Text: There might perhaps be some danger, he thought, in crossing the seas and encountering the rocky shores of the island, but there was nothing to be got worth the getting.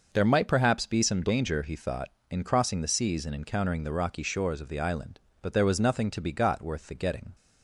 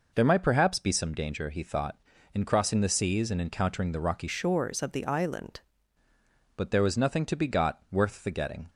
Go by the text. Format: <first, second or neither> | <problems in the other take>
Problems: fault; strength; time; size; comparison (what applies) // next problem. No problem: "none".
first | changes voice from "shores" to "island"; from 4.2 to 5.5 s; 1.3 s long